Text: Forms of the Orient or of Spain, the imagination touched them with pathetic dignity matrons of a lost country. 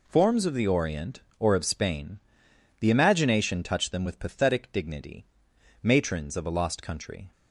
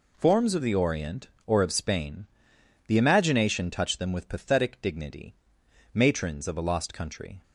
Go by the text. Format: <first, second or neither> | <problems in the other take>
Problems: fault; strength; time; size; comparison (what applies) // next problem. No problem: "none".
neither | pauses between "dignity" and "matrons"; noticeable; the same in both